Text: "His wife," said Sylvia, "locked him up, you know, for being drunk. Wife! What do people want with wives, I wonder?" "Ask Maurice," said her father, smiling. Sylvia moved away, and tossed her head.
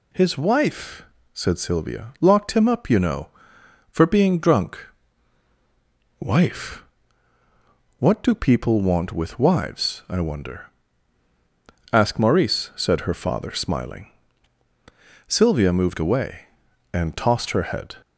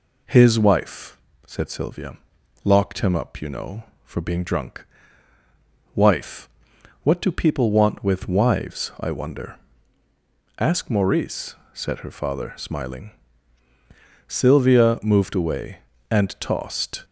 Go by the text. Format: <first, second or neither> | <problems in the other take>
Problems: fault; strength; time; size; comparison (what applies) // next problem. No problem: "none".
first | stops before "her head"; at 17.0 s